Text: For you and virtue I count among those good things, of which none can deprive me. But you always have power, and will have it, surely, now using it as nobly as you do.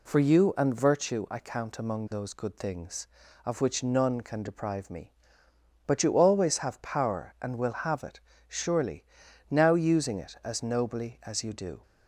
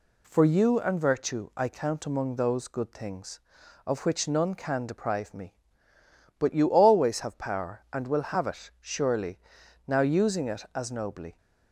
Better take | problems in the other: first | stops before "as you do"; at 11.3 s

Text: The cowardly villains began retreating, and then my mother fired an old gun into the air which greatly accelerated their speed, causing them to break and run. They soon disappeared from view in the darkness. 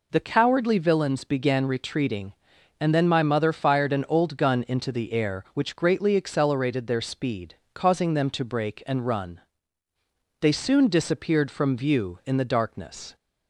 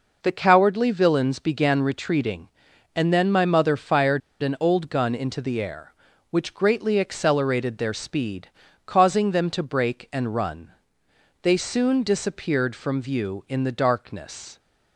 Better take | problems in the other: first | pauses between "fired" and "an"; slight; at 4.2 s; 0.22 s long

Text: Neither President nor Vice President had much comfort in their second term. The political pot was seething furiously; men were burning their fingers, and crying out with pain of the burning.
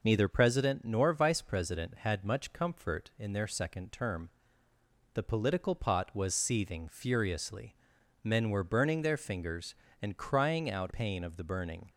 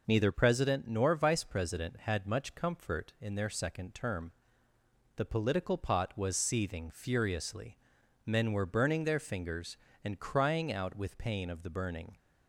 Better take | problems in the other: second | skips "with"; at 10.9 s

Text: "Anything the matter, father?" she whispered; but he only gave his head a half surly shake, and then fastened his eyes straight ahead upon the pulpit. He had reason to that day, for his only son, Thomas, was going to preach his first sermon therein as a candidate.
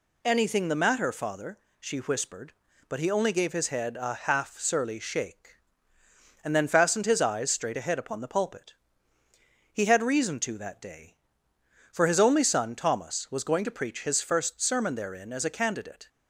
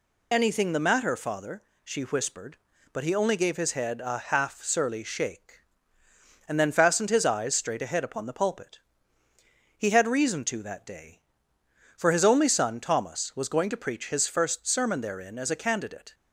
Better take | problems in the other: first | loses the start of "Anything"; at 0.3 s; 30 ms

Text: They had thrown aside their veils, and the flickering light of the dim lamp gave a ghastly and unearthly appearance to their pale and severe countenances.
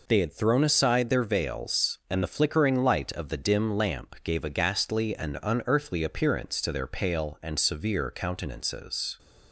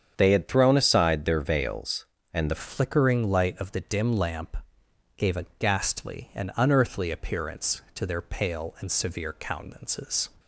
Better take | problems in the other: first | starts louder than the rest; strong; until 1.1 s; 8 dB // changes voice at "flickering"; from 2.5 s on; 7.7 s long // pauses between "lamp" and "gave"; noticeable; at 4.5 s; 0.60 s long

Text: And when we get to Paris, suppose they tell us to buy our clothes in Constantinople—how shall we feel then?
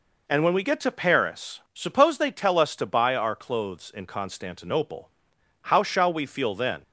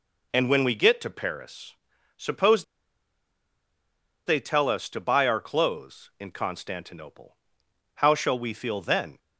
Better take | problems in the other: first | pauses between "suppose" and "they"; strong; at 2.6 s; 1.6 s long

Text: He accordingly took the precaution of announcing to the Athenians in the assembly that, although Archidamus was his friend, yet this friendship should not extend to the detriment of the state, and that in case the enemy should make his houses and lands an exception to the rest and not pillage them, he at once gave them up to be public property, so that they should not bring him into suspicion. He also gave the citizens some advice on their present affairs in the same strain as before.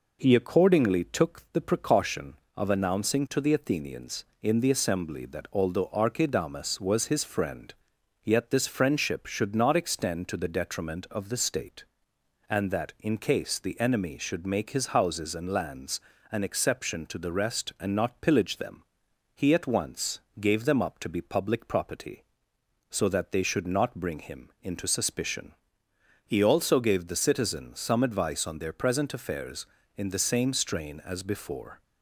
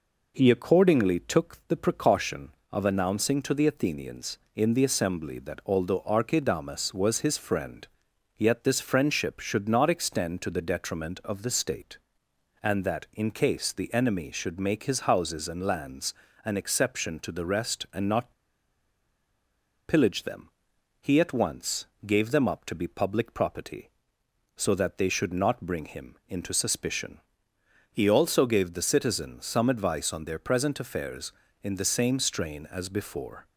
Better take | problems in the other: first | pauses between "lands" and "an"; slight; at 16.1 s; 0.30 s long; slight in the first // pauses between "not" and "pillage"; strong; at 18.3 s; 1.5 s long // pauses between "once" and "gave"; slight; at 21.8 s; 0.18 s long; slight in the first

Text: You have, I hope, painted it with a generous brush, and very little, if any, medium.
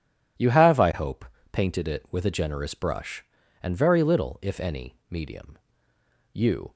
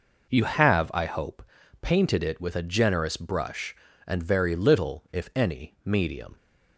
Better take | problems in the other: second | goes on to say "You"; slight; from 6.3 s on; 0.40 s long

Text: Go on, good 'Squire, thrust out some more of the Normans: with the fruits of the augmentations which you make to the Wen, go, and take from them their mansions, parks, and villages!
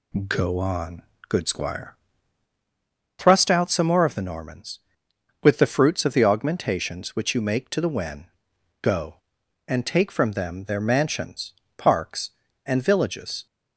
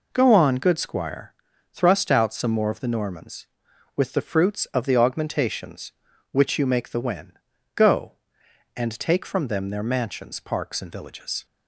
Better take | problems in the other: first | skips "to"; at 6.8 s

